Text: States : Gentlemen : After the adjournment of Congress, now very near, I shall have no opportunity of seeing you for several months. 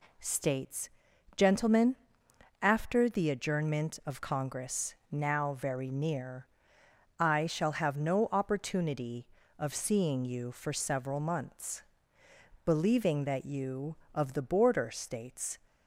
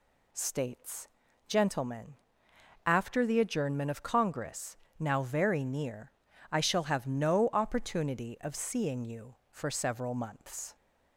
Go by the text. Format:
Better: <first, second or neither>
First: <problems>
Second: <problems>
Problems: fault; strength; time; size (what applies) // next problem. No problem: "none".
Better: second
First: goes on to say "Believing that you of the border States"; strong; from 12.6 s on; 2.9 s long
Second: none